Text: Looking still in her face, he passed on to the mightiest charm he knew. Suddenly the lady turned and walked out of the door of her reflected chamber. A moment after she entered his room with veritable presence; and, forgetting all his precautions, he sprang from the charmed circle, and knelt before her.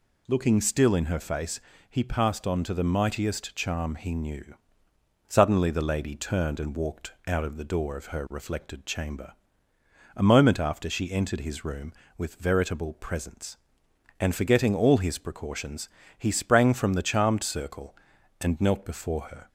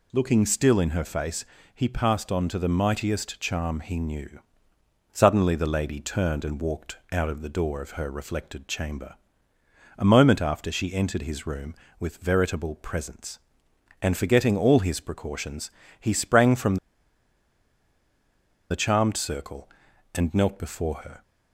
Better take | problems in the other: first | pauses between "walked" and "out"; slight; at 6.9 s; 0.16 s long; slight in the first // pauses between "from" and "the"; strong; at 16.7 s; 1.9 s long

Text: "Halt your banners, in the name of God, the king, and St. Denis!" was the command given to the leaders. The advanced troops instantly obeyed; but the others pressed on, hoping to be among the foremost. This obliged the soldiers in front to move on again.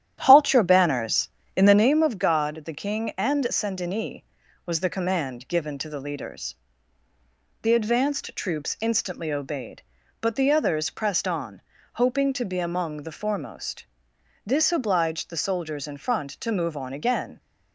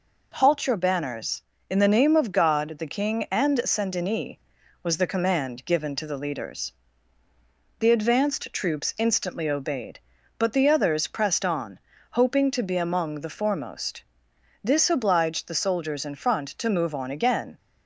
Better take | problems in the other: second | starts louder than the rest; strong; until 1.9 s; 11 dB

